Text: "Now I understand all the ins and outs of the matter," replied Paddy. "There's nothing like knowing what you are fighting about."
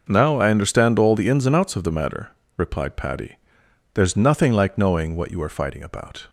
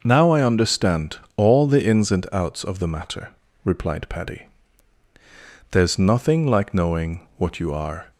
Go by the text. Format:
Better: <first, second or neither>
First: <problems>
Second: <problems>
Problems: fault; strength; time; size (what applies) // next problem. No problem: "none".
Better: first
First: none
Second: pauses between "understand" and "all"; slight; at 1.1 s; 0.18 s long // stops before "fighting about"; at 8.1 s